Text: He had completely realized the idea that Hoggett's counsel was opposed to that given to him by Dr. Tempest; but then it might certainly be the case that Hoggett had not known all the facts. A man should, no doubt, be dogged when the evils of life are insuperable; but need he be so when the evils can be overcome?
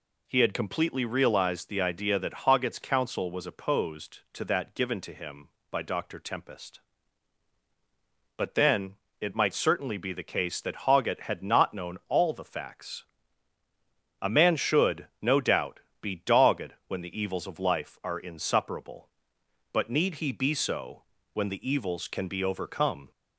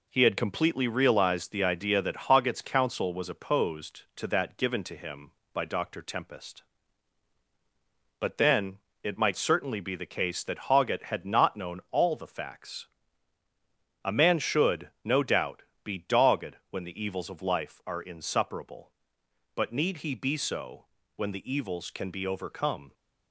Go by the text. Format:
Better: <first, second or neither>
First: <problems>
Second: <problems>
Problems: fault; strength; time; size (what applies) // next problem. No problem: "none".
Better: first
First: pauses between "then" and "it"; slight; at 8.9 s; 0.24 s long // pauses between "so" and "when"; slight; at 21.0 s; 0.30 s long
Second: gets quieter; noticeable; throughout; 4.5 dB // pauses between "then" and "it"; slight; at 8.7 s; 0.24 s long // pauses between "so" and "when"; slight; at 20.8 s; 0.30 s long